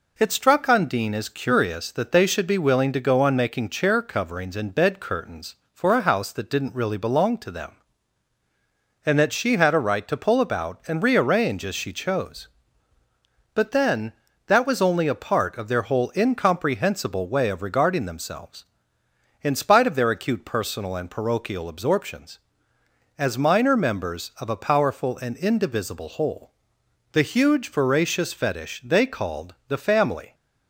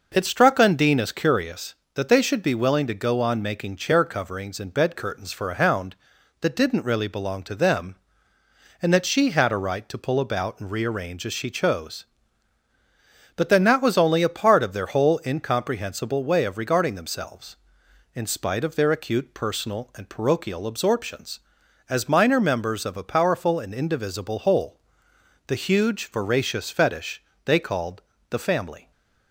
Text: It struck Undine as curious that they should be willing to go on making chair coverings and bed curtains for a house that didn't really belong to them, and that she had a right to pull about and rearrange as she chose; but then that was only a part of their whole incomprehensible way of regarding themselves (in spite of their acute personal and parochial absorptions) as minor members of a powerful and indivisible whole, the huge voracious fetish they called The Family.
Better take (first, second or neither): first